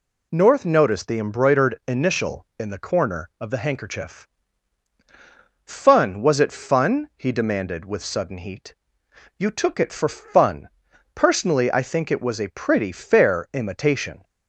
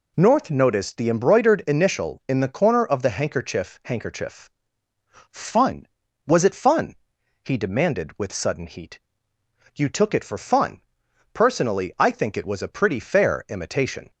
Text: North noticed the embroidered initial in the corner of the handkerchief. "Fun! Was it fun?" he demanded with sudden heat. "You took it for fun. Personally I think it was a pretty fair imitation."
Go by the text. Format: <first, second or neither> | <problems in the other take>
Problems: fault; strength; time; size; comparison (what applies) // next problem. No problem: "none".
first | says "handkerchief" twice; at 3.8 s